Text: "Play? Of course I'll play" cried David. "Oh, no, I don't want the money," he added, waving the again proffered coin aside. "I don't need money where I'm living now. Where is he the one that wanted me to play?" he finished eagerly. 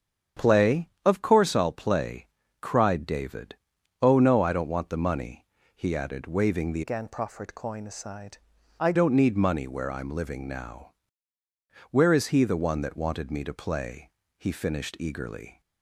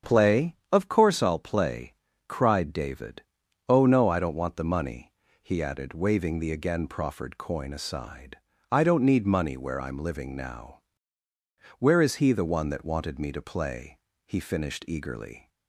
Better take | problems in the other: second | starts louder than the rest; strong; until 1.5 s; 8 dB; strong in the second // pauses between "play" and "cried"; slight; at 2.2 s; 0.34 s long; slight in the second // changes voice from "again" to "I"; from 6.8 to 8.9 s; 2.1 s long

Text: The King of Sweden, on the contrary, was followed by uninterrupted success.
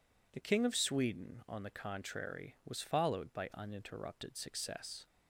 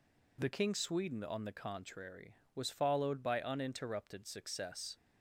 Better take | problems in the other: first | skips "of"; at 0.7 s

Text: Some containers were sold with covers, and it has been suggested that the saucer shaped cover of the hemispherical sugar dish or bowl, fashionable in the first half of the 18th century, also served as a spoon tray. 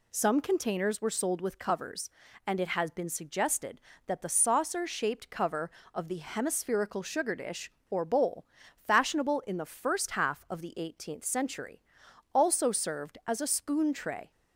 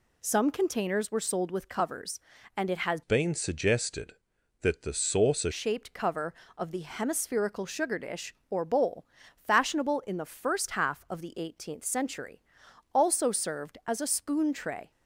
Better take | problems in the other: first | changes voice from "been" to "saucer"; from 3.0 to 5.5 s; 2.5 s long

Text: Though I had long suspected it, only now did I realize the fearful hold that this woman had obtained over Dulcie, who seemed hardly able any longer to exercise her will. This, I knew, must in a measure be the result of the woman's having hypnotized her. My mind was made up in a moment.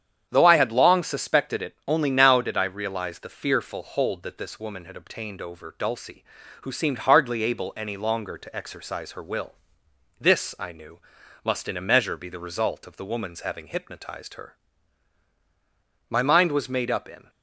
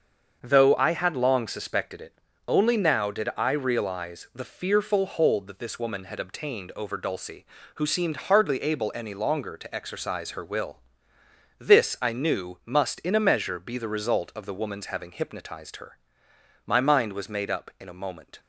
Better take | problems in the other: second | starts louder than the rest; strong; until 1.3 s; 8.5 dB; also in the second // stops before "a moment"; at 17.2 s

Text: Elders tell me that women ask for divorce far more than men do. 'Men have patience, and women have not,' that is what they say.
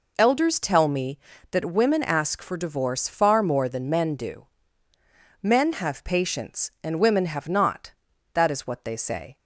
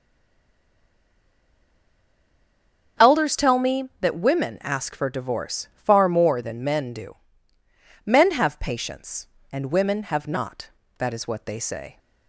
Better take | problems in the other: first | stays silent before the first word; strong; until 2.9 s; 2.9 s long // starts louder than the rest; strong; until 4.1 s; 7.5 dB

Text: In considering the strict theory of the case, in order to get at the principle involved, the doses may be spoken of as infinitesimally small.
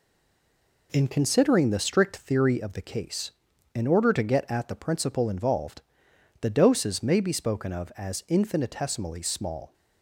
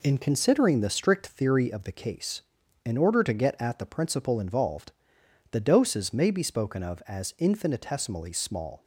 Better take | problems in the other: second | stays silent before the first word; slight; until 0.9 s; 0.9 s long

